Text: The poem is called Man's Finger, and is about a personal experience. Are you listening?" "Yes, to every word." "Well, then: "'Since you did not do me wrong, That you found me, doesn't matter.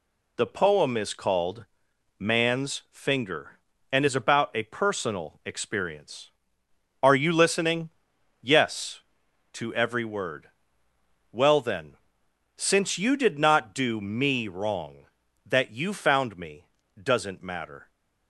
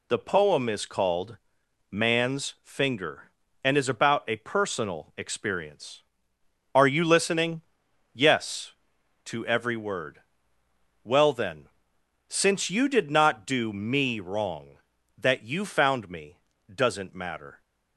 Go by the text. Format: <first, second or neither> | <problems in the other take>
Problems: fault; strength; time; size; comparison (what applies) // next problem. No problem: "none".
neither | pauses between "called" and "Man's"; noticeable; the same in both